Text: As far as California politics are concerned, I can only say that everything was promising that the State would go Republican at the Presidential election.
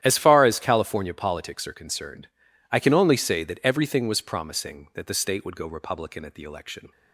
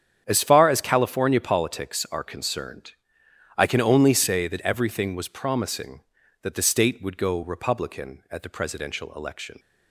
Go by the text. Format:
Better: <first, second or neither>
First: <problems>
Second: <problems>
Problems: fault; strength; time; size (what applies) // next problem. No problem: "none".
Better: second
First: starts louder than the rest; strong; until 1.0 s; 11 dB // skips "Presidential"; at 6.4 s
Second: starts louder than the rest; strong; until 1.2 s; 8.5 dB